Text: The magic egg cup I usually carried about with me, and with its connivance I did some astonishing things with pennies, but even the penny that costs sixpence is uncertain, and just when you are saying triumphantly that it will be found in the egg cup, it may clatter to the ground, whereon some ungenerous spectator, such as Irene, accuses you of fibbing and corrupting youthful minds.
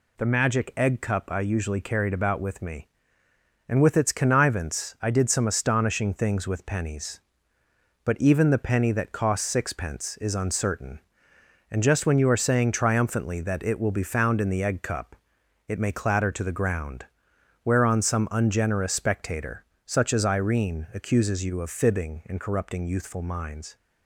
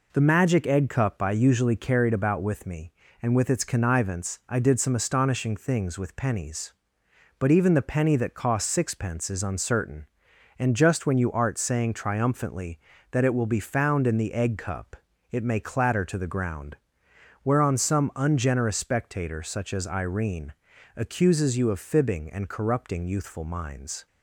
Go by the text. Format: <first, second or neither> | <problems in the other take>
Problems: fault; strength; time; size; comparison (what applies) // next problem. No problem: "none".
first | says "art" for "are"; at 11.3 s